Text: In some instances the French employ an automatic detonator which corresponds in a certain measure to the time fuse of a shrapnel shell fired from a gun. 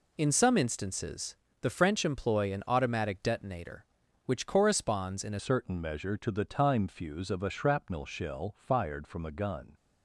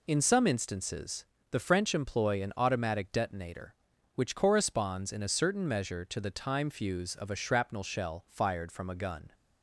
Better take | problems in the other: second | pauses between "instances" and "the"; slight; at 1.3 s; 0.26 s long; slight in the second // changes voice at "certain"; from 5.3 s on; 4.4 s long

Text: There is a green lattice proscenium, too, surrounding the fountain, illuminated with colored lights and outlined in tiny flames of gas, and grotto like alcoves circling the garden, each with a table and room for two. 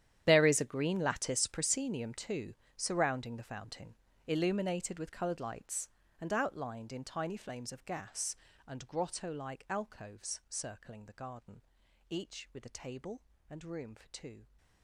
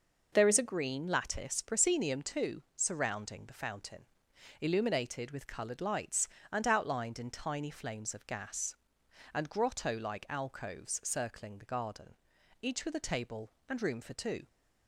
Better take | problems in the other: second | gets quieter; strong; throughout; 17.5 dB

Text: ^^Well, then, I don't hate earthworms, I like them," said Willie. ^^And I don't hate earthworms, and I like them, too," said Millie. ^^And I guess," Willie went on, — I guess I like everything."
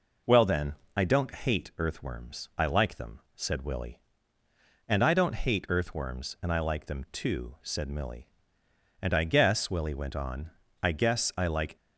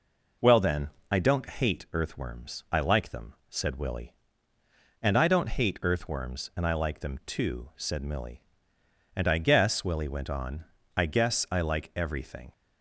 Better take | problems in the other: second | stops before "everything"; at 11.7 s

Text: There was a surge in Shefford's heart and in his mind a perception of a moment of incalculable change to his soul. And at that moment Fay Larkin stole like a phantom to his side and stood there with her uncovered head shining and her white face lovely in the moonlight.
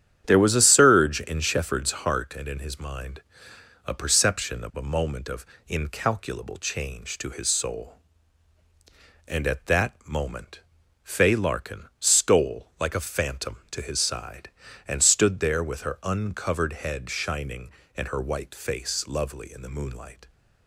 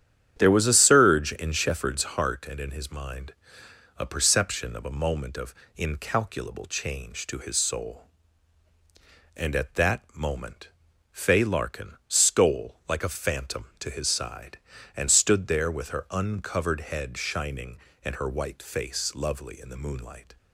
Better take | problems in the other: neither | starts louder than the rest; strong; the same in both // pauses between "mind" and "a"; noticeable; the same in both // pauses between "of" and "incalculable"; slight; the same in both // pauses between "moment" and "Fay"; the same in both

